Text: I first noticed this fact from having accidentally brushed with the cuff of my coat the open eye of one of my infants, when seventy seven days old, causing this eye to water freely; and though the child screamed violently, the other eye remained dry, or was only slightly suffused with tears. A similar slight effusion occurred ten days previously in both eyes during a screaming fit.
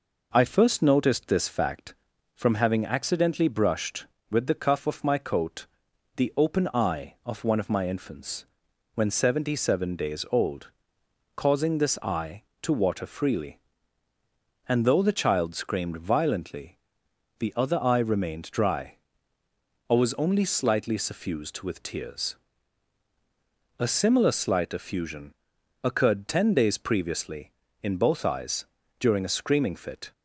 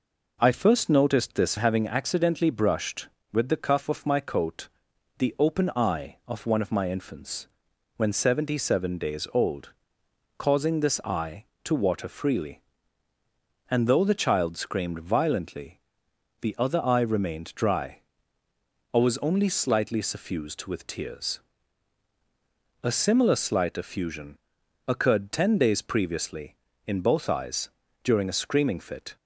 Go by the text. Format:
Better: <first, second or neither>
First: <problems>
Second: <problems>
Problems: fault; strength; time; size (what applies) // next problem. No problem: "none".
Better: first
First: pauses between "coat" and "the"; noticeable; at 5.6 s; 0.50 s long // pauses between "effusion" and "occurred"; noticeable; at 25.3 s; 0.48 s long // pauses between "eyes" and "during"; slight; at 28.6 s; 0.36 s long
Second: skips "fact from"; at 1.5 s // pauses between "coat" and "the"; noticeable; at 4.6 s; 0.50 s long // pauses between "effusion" and "occurred"; noticeable; at 24.3 s; 0.48 s long // pauses between "eyes" and "during"; slight; at 27.6 s; 0.36 s long